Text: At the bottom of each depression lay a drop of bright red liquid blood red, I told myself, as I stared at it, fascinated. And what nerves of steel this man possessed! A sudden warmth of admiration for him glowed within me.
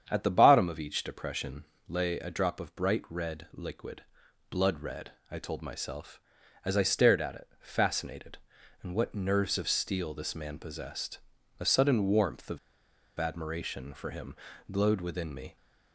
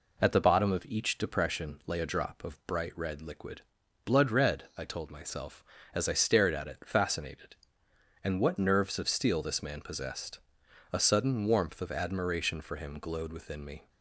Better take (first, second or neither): second